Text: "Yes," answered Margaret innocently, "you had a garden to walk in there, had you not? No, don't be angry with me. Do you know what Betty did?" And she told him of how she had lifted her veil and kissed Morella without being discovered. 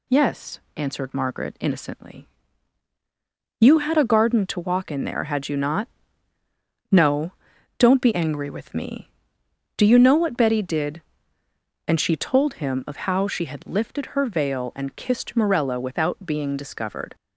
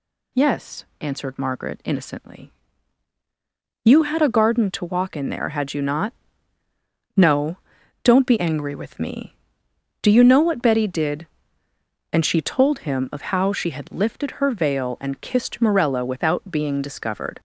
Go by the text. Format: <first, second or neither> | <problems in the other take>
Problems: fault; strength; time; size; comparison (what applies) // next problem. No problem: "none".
first | gets louder; slight; throughout; 2 dB